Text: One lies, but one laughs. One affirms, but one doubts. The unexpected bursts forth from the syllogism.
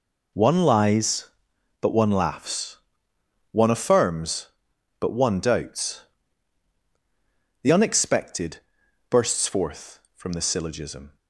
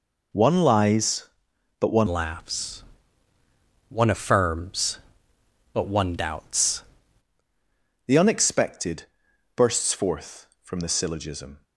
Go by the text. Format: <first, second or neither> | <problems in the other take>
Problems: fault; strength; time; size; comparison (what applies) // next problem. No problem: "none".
first | changes voice from "laughs" to "doubts"; from 2.0 to 6.8 s; 4.8 s long // pauses between "unexpected" and "bursts"; noticeable; at 9.0 s; 0.52 s long; noticeable in the first